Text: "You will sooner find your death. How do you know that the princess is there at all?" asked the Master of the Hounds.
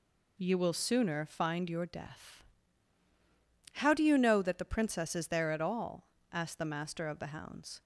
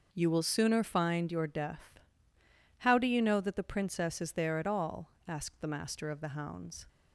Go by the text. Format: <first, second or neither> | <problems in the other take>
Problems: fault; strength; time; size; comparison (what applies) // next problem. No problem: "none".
neither | none